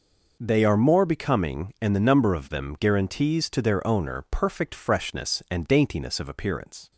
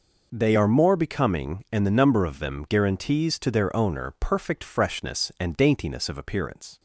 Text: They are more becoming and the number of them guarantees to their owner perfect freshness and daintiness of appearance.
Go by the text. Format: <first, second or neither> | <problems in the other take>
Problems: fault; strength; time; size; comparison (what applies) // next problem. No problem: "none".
neither | none